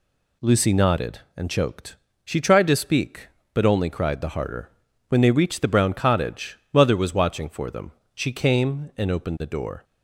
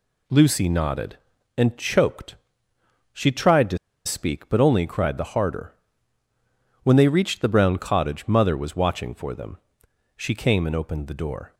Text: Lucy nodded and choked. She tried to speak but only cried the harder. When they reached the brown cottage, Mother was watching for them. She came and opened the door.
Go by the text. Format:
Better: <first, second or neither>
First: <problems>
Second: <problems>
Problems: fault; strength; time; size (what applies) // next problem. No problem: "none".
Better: first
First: none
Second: pauses between "to" and "speak"; slight; at 3.7 s; 0.28 s long